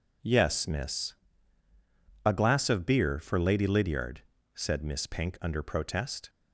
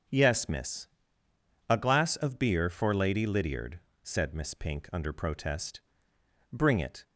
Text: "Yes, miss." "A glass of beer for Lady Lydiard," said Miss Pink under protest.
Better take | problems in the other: first | starts louder than the rest; until 1.9 s; 6 dB // goes on to say "Bring it"; from 6.5 s on; 0.50 s long

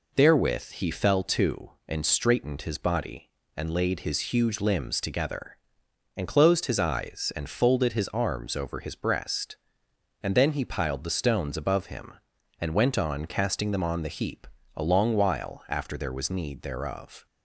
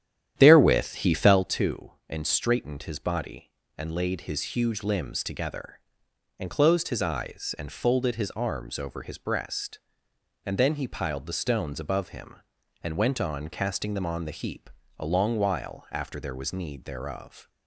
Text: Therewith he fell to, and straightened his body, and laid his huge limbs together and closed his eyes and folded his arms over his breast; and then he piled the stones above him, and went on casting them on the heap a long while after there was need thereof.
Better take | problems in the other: first | starts louder than the rest; strong; until 1.5 s; 10.5 dB // pauses between "heap" and "a"; slight; at 14.6 s; 0.30 s long; slight in the first

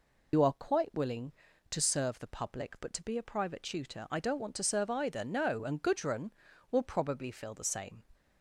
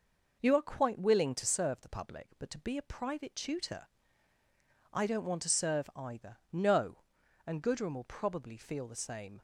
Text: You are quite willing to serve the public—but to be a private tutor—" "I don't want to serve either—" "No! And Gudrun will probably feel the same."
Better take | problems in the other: second | loses the start of "You"; at 0.3 s; 85 ms

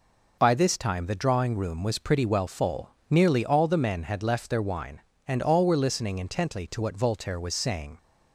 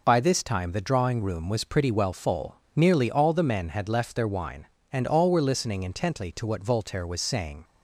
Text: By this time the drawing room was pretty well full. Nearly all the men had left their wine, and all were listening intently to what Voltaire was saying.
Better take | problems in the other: neither | none

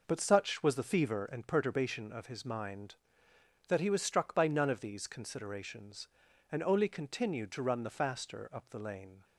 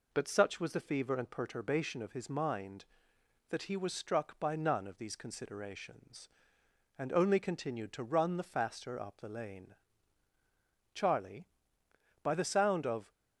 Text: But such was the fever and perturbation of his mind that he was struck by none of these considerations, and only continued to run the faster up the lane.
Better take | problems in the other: first | goes on to say "Charlie by the sound of"; strong; from 10.9 s on; 2.1 s long

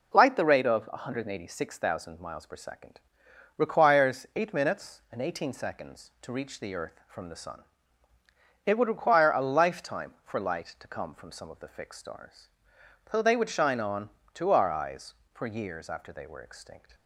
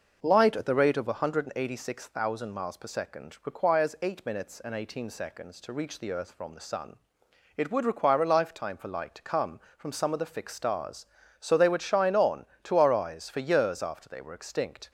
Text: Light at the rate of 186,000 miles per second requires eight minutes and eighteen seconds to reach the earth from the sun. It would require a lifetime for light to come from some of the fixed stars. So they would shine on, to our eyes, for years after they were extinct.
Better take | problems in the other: second | skips "at"; at 0.3 s // pauses between "second" and "requires"; noticeable; at 3.0 s; 0.56 s long

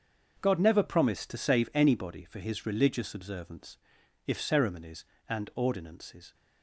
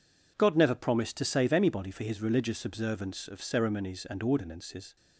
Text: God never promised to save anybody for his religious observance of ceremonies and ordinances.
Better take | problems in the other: second | starts louder than the rest; until 1.4 s; 6.5 dB // says "if" for "of"; at 4.2 s

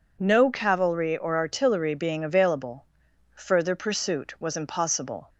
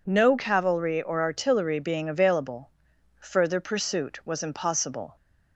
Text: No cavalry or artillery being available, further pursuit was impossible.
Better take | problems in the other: neither | none

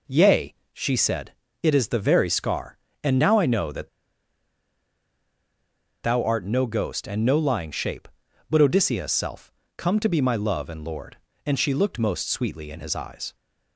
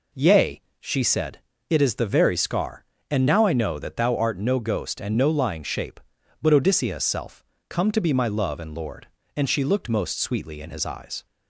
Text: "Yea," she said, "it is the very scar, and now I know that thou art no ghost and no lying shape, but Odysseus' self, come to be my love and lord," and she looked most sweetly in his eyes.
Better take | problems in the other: second | pauses between "that" and "thou"; strong; at 3.8 s; 2.1 s long

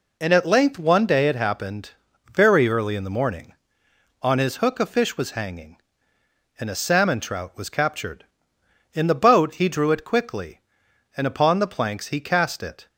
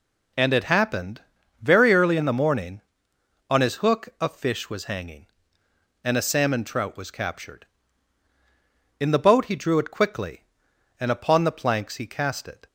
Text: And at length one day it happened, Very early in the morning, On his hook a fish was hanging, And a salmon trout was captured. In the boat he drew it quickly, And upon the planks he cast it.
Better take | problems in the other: first | skips "at length one day"; at 0.5 s

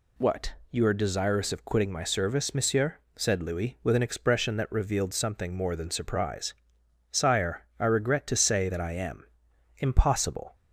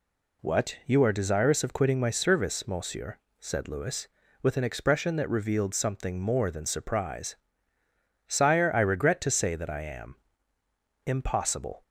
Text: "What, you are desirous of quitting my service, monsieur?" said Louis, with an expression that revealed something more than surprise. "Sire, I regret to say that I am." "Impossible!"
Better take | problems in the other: neither | none

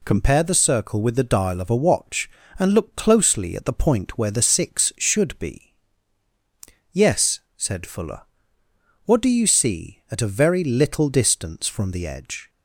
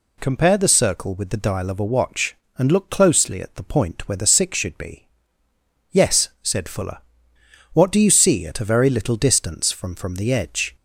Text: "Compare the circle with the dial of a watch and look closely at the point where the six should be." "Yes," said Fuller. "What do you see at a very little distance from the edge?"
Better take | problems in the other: first | says "from" twice; at 9.9 s

